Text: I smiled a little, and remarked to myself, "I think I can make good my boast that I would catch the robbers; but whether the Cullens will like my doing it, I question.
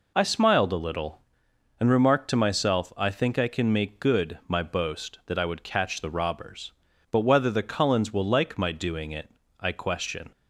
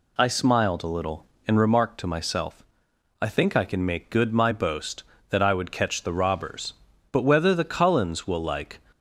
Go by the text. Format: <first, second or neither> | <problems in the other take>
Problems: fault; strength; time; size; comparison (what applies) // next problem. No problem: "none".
first | stops before "my doing it I question"; at 8.9 s